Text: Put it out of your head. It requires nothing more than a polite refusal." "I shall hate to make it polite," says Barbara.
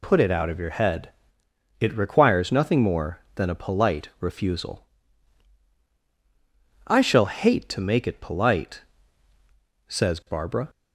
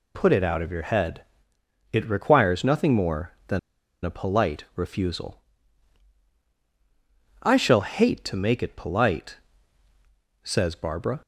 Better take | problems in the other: first | pauses between "than" and "a"; at 3.5 s; 0.43 s long

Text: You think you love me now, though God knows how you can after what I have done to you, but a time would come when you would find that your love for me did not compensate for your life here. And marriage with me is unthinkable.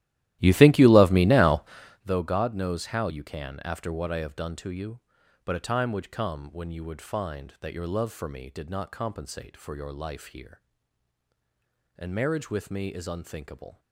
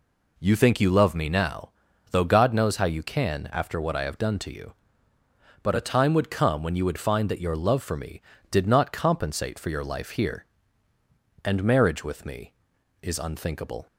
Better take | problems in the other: second | starts louder than the rest; strong; until 2.1 s; 14.5 dB

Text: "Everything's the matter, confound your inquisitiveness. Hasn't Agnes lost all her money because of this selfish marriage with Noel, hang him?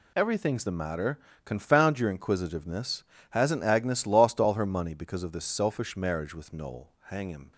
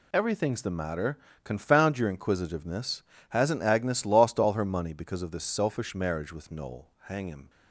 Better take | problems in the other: neither | none

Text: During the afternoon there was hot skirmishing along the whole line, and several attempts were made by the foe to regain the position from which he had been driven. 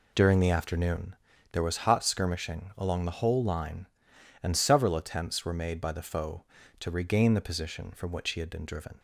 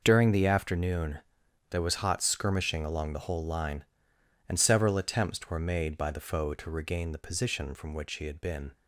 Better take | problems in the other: first | pauses between "afternoon" and "there"; noticeable; at 1.1 s; 0.50 s long; also in the first // stops before "driven"; at 8.7 s

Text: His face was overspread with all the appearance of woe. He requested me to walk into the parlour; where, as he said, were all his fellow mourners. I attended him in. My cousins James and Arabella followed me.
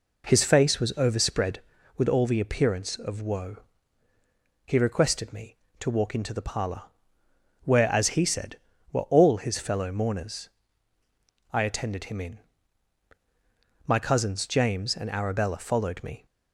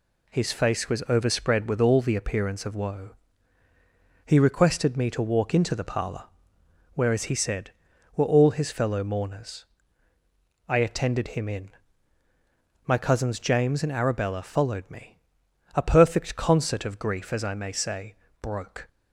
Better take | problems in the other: first | goes on to say "A perfect concert of grief as I may say broke"; strong; from 15.7 s on; 3.1 s long

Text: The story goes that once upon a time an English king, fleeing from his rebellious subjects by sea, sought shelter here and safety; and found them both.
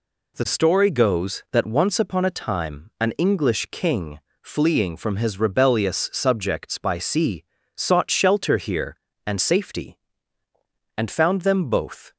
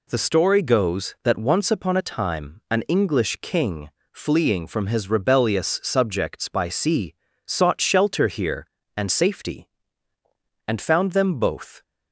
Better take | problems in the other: neither | none

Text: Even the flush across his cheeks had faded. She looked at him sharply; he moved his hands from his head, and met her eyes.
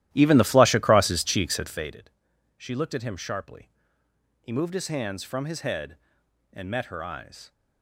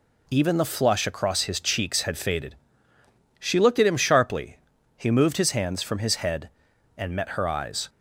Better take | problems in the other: second | starts louder than the rest; strong; until 2.0 s; 14 dB

